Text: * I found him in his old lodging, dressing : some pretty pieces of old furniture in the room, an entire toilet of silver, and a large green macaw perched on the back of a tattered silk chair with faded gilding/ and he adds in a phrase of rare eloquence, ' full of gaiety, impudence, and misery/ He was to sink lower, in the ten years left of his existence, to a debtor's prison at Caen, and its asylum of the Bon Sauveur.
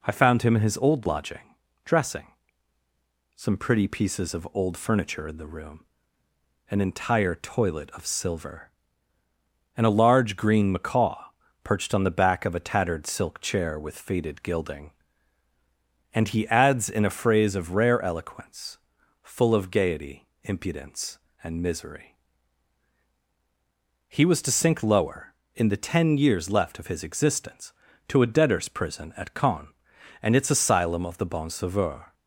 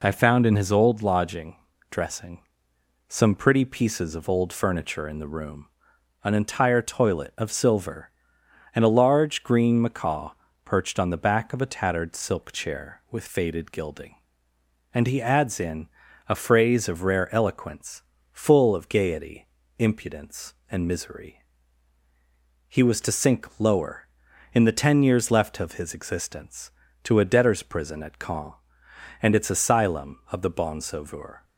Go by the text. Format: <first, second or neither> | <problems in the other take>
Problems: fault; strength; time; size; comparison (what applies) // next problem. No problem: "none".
first | skips "him"; at 0.4 s // pauses between "macaw" and "perched"; slight; at 10.3 s; 0.34 s long; also in the first // pauses between "in" and "a"; at 15.8 s; 0.42 s long